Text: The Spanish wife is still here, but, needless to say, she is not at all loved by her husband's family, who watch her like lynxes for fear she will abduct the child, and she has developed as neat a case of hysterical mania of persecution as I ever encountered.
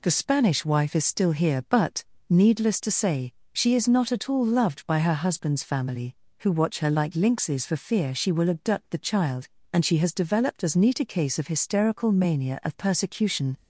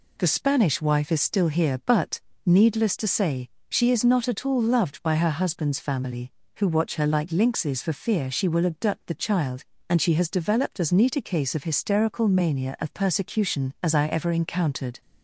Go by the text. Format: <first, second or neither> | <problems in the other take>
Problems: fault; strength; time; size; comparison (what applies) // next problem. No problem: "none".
second | stops before "as I ever encountered"; at 13.5 s